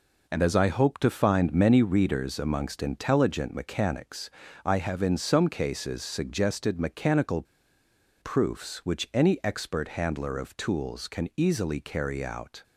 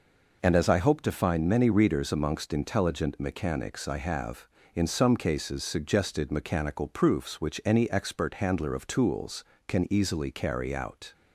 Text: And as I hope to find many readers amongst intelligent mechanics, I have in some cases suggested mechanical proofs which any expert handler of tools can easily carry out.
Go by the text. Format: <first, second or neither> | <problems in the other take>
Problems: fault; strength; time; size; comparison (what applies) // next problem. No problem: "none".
second | pauses between "mechanical" and "proofs"; noticeable; at 7.4 s; 0.78 s long